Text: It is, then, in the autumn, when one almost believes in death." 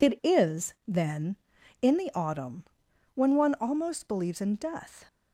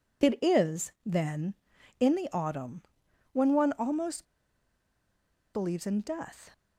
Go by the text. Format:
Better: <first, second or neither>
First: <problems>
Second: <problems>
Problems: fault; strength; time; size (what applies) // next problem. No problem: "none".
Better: first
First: none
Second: pauses between "almost" and "believes"; strong; at 4.2 s; 1.2 s long